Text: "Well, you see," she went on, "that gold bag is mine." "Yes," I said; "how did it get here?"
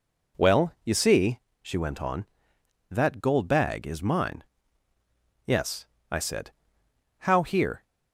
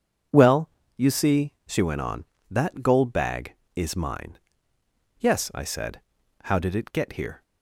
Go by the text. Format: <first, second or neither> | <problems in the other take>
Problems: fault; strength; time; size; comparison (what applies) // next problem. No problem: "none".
second | skips "did it get"; at 7.4 s